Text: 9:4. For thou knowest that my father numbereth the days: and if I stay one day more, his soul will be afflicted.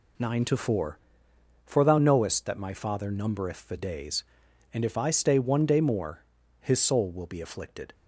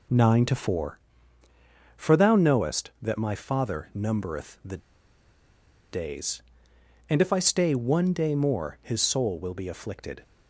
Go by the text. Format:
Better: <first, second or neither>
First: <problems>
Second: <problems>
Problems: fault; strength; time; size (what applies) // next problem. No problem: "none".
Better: first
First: none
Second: pauses between "the" and "days"; at 4.7 s; 1.1 s long